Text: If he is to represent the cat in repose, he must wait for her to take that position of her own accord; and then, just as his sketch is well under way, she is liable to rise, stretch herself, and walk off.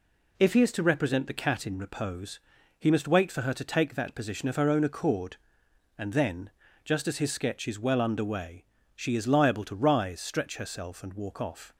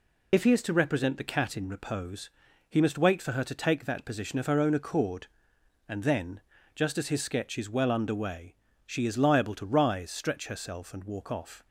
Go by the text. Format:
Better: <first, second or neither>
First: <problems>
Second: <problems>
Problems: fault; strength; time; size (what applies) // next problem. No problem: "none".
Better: first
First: none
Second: loses the start of "If"; at 0.3 s; 55 ms